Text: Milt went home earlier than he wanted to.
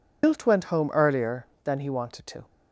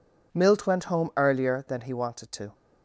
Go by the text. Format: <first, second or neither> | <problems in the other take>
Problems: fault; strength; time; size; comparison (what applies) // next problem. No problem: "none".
second | loses the start of "Milt"; at 0.2 s; 125 ms